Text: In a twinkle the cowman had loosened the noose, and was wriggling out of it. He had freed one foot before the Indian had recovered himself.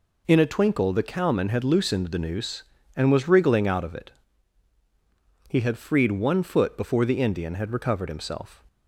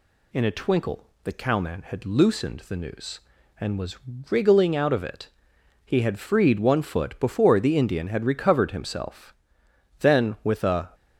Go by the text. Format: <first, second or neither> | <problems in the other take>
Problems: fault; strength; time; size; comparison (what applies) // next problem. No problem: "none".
first | pauses between "twinkle" and "the"; slight; at 1.0 s; 0.16 s long // pauses between "was" and "wriggling"; slight; at 3.9 s; 0.32 s long // goes on to say "Then with a"; noticeable; from 10.0 s on; 0.92 s long